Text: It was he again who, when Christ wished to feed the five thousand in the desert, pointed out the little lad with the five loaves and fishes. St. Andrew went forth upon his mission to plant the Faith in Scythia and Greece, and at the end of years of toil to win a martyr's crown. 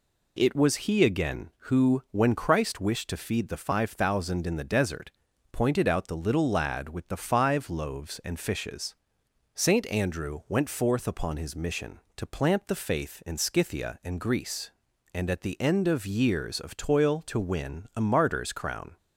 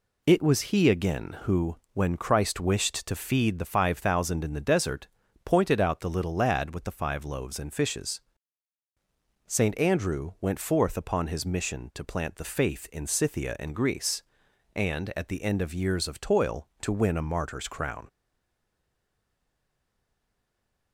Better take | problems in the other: first | stays silent after the last word; strong; from 18.0 s on; 2.9 s long

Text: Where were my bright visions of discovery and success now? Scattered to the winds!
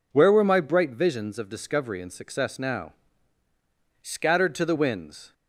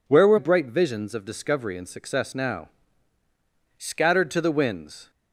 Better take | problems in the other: first | skips "my"; at 0.3 s

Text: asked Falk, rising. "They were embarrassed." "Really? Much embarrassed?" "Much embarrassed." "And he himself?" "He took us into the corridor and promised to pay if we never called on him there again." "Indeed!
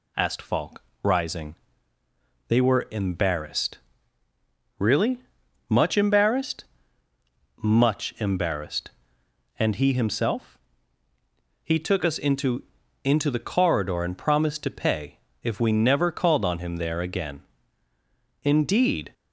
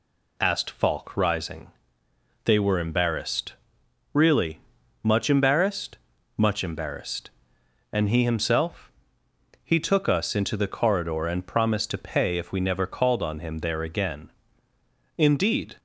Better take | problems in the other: second | says "into" twice; at 13.0 s // pauses between "pay" and "if"; slight; at 15.1 s; 0.24 s long

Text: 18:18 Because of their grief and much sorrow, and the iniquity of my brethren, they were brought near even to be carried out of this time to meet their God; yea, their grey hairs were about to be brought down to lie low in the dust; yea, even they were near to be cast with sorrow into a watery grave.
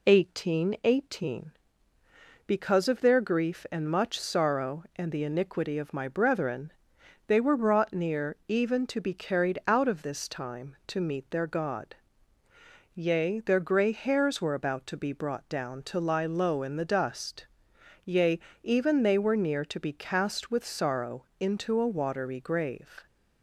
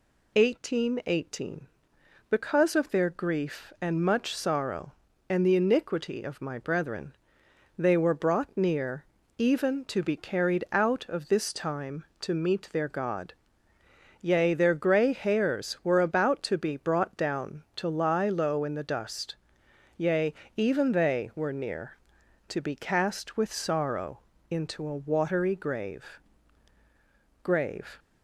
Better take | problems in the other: first | pauses between "near" and "even"; slight; at 9.0 s; 0.34 s long // pauses between "sorrow" and "into"; slight; at 24.1 s; 0.32 s long; slight in the first // says "grave" twice; at 27.4 s

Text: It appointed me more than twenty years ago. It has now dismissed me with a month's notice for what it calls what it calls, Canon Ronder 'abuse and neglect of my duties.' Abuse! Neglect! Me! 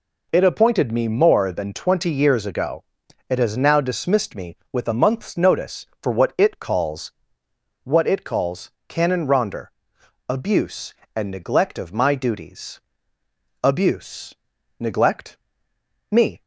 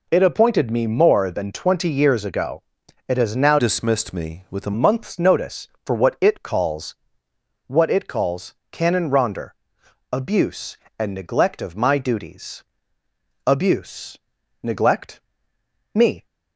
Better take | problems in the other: first | changes voice from "dismissed" to "a"; from 3.5 to 4.7 s; 1.2 s long // pauses between "calls" and "what"; noticeable; at 6.9 s; 0.72 s long; noticeable in the first // pauses between "Ronder" and "abuse"; noticeable; at 9.5 s; 0.60 s long; noticeable in the first

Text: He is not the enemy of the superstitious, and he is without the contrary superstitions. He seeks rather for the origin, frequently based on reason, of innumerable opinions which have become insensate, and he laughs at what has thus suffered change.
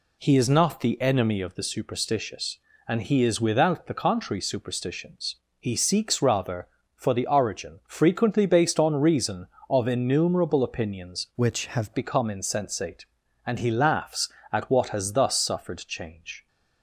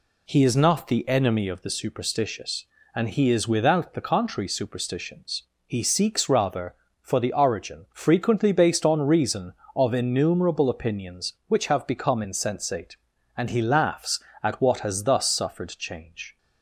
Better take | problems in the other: second | changes voice from "which" to "have"; from 11.3 to 11.9 s; 0.6 s long

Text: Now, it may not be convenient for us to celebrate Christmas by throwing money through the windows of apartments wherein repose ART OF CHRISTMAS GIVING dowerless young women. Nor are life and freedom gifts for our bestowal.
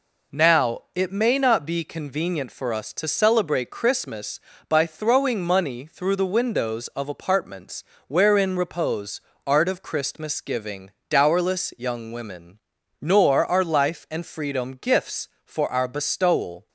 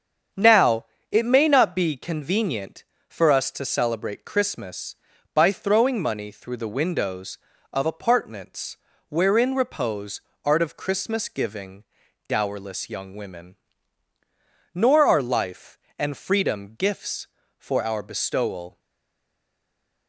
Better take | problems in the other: first | starts louder than the rest; strong; until 1.6 s; 7.5 dB // pauses between "apartments" and "wherein"; slight; at 8.7 s; 0.32 s long; slight in the first // pauses between "repose" and "ART"; slight; at 10.2 s; 0.22 s long; slight in the first // pauses between "GIVING" and "dowerless"; at 11.8 s; 0.44 s long; slight in the first // stays silent after the last word; noticeable; from 18.7 s on; 1.3 s long

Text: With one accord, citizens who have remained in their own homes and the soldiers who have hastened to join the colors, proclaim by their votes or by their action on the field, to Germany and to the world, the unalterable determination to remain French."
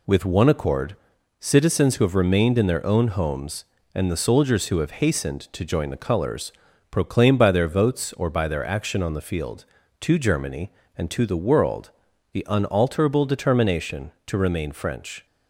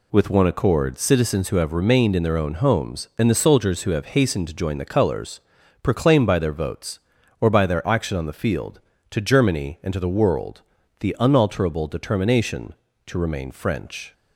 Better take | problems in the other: neither | none

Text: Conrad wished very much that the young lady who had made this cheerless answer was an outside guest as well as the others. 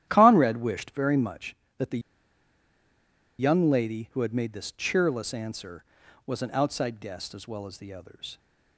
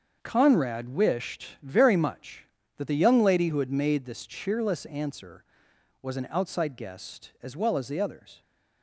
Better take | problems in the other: second | starts louder than the rest; strong; until 1.0 s; 11.5 dB; also in the second // pauses between "the" and "young"; strong; at 1.9 s; 1.4 s long

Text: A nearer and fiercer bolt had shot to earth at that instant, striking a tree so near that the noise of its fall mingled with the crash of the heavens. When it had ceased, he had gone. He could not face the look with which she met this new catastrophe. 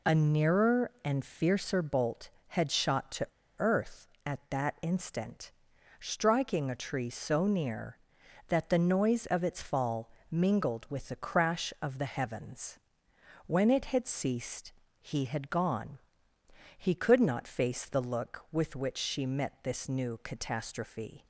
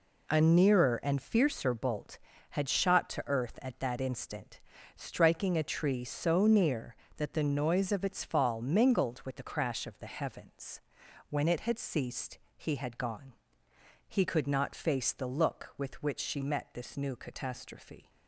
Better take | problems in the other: second | pauses between "to" and "earth"; slight; at 3.2 s; 0.31 s long // pauses between "fall" and "mingled"; slight; at 10.1 s; 0.18 s long

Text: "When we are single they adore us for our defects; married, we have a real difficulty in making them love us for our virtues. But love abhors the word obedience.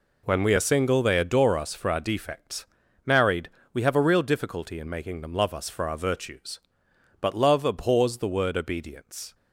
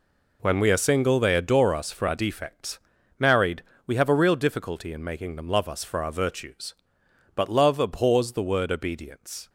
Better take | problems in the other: neither | none

